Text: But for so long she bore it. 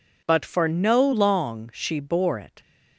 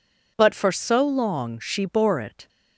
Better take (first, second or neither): second